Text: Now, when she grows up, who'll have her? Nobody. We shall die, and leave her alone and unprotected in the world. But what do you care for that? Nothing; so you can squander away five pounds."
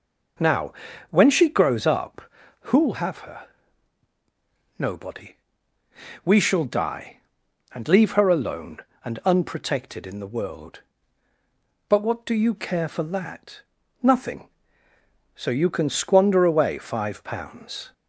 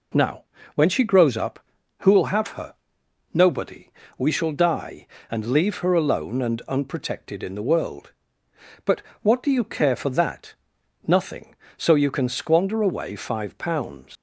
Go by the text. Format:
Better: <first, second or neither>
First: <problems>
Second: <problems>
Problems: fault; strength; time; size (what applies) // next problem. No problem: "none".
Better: first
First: none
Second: pauses between "But" and "what"; slight; at 9.0 s; 0.22 s long // leaves "pounds" unfinished; at 14.1 s; 95 ms